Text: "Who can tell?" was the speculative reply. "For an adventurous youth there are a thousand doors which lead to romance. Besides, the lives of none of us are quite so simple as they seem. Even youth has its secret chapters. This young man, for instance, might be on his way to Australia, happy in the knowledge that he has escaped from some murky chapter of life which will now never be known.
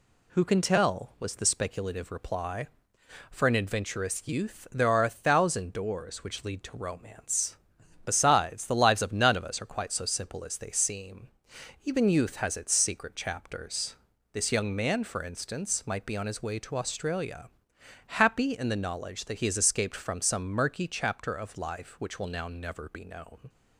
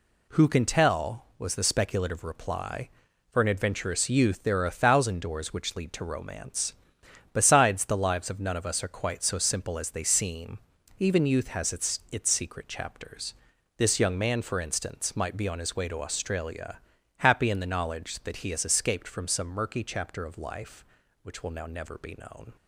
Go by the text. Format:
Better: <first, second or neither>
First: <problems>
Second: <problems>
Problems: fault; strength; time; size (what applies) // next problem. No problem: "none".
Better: first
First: none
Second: says "its" twice; at 12.0 s